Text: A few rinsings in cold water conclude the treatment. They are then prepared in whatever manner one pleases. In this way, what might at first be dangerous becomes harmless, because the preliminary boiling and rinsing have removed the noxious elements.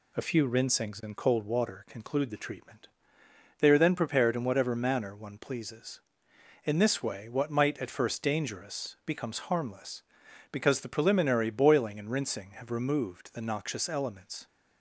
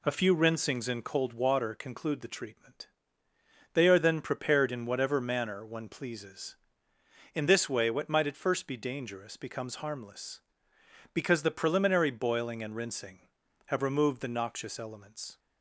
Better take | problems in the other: second | skips "be"; at 8.2 s

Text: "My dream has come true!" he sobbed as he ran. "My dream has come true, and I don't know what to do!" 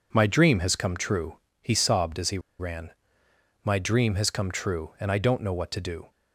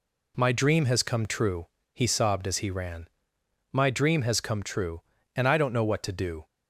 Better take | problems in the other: second | pauses between "he" and "ran"; slight; at 2.3 s; 0.20 s long

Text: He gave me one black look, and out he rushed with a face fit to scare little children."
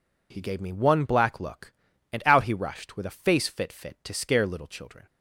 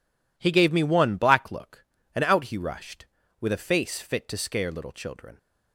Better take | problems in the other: second | says "fit" twice; at 3.7 s

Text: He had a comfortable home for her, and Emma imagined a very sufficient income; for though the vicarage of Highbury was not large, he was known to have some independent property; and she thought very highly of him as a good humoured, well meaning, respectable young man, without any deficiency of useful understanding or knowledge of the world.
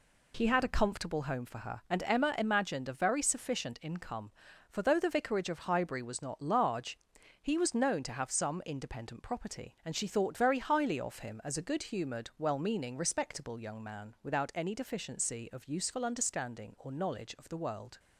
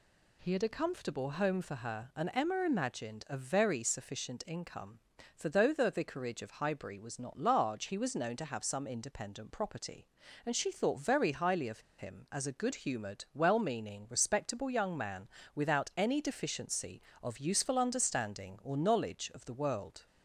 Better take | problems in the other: first | pauses between "of" and "him"; slight; at 11.7 s; 0.18 s long

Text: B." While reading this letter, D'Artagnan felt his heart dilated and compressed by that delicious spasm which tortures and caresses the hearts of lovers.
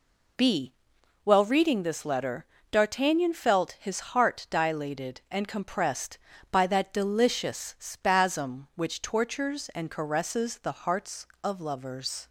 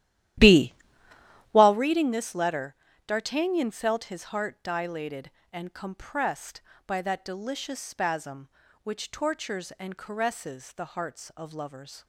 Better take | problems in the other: first | starts louder than the rest; strong; until 1.8 s; 13 dB

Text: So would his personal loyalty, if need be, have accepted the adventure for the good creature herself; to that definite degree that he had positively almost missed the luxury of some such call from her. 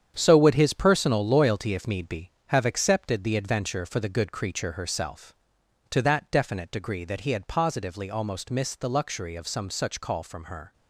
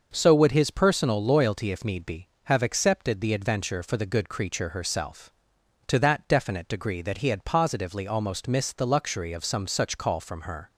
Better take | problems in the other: second | gets quieter; strong; throughout; 9 dB // starts louder than the rest; strong; until 1.1 s; 8.5 dB; also in the second

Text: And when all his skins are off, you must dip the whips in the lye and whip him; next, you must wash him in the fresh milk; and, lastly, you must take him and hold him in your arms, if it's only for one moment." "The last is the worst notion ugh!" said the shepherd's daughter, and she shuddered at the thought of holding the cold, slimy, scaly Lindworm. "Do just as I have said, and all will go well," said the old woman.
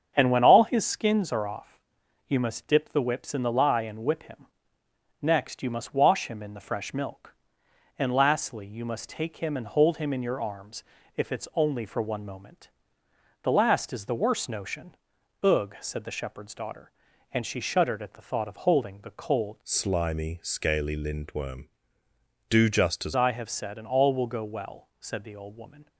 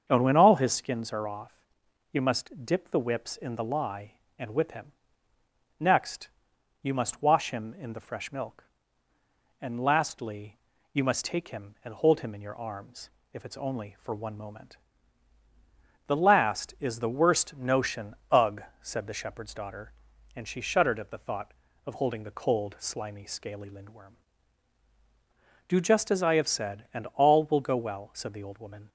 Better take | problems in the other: second | starts louder than the rest; strong; until 1.1 s; 7.5 dB; also in the second // pauses between "notion" and "ugh"; noticeable; at 14.9 s; 0.48 s long // changes voice from "slimy" to "as"; from 19.6 to 23.1 s; 3.5 s long

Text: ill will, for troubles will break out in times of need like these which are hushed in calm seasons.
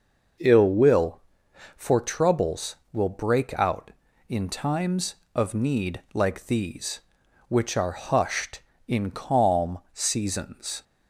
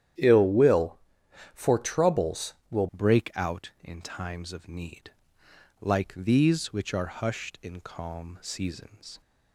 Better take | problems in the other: first | starts louder than the rest; strong; until 1.7 s; 10.5 dB // changes voice at "break"; from 2.9 s on; 6.3 s long // pauses between "need" and "like"; noticeable; at 5.1 s; 0.72 s long

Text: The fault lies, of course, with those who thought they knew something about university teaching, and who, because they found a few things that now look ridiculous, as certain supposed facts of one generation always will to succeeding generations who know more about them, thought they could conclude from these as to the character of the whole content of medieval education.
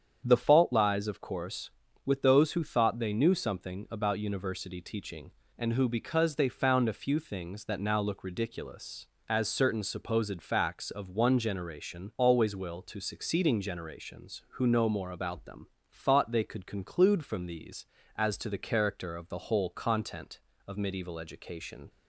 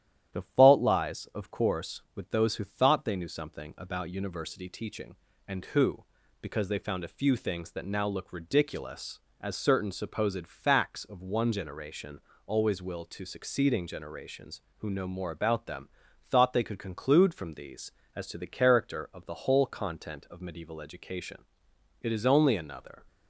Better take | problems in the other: first | starts louder than the rest; strong; until 1.4 s; 11 dB; strong in the first // pauses between "generation" and "always"; slight; at 12.1 s; 0.26 s long // goes on to say "It is only another"; noticeable; from 22.0 s on; 0.96 s long

